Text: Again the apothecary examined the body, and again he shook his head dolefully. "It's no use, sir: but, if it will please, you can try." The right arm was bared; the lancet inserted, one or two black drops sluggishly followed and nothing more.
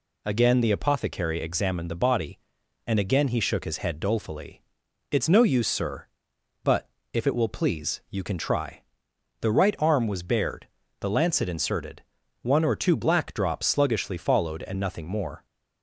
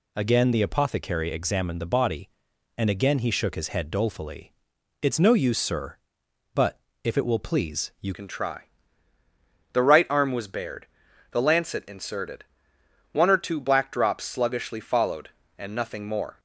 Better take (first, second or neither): first